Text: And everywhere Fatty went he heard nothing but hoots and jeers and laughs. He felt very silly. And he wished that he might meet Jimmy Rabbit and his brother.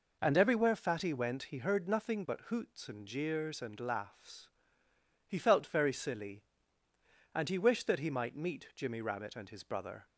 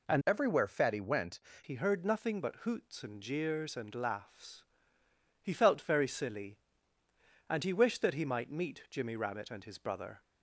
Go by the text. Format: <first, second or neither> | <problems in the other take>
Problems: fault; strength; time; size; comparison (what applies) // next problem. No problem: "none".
first | changes voice from "everywhere" to "went"; from 0.2 to 1.4 s; 1.2 s long